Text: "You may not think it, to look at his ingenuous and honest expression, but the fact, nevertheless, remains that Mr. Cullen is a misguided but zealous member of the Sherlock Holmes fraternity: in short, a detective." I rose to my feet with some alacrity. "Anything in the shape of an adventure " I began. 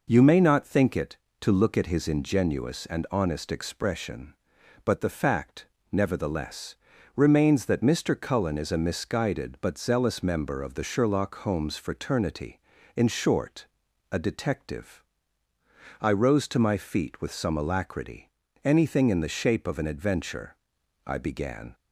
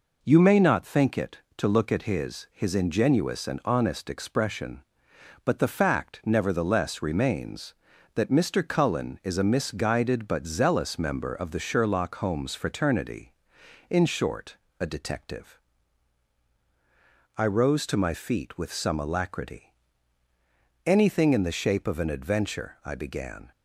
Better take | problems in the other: first | says "his" twice; at 2.5 s

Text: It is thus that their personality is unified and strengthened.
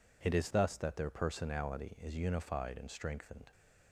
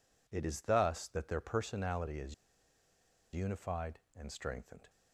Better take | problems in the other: first | pauses between "is" and "unified"; at 2.3 s; 0.98 s long

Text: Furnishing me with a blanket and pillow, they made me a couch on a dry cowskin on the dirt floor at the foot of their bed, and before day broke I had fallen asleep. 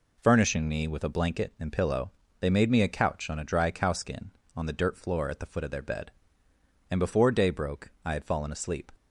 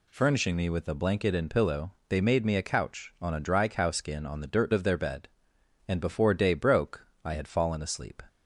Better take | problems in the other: first | skips "floor at the foot"; at 4.7 s // pauses between "broke" and "I"; slight; at 7.0 s; 0.18 s long

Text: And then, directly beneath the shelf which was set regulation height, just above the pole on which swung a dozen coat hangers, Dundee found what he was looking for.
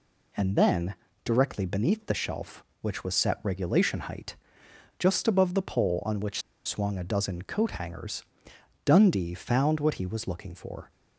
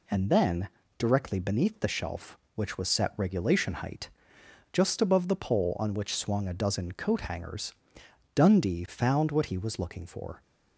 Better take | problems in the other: second | pauses between "which" and "swung"; slight; at 6.4 s; 0.24 s long

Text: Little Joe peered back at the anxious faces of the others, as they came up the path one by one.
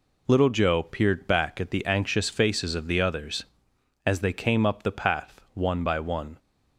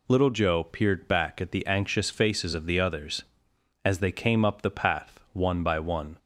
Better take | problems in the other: second | gets quieter; throughout; 7 dB

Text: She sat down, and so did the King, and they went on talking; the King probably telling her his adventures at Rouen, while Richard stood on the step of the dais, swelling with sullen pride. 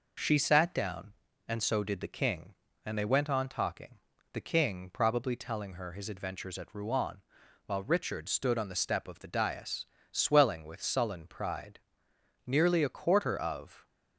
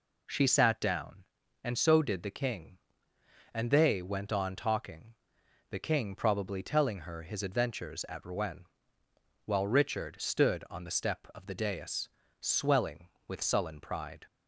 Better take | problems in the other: second | goes on to say "Nearly a quarter of"; from 12.4 s on; 1.4 s long

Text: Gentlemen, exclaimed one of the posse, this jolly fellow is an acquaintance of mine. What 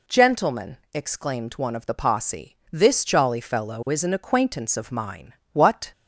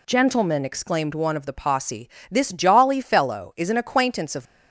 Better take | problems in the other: first | stops before "mine What"; at 4.4 s

